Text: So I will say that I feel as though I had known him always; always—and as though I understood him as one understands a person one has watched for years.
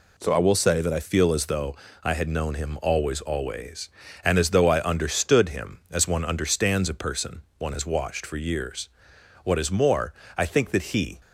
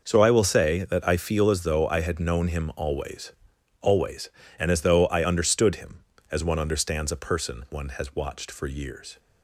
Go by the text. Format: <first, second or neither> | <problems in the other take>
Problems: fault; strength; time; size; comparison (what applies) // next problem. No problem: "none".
second | pauses between "though" and "I"; slight; at 1.7 s; 0.28 s long // pauses between "person" and "one"; slight; at 7.4 s; 0.16 s long // goes on to say "What is more I think that he"; strong; from 9.4 s on; 1.7 s long